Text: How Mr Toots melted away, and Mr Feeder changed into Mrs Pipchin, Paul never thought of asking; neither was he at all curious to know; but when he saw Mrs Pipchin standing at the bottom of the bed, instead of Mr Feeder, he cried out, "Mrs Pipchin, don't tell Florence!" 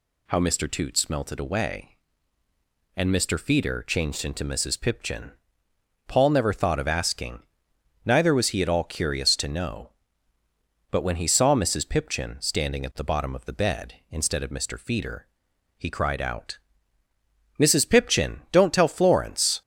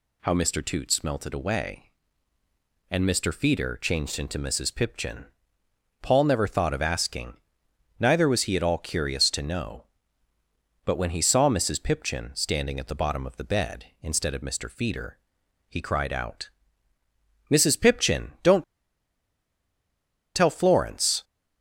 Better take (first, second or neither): first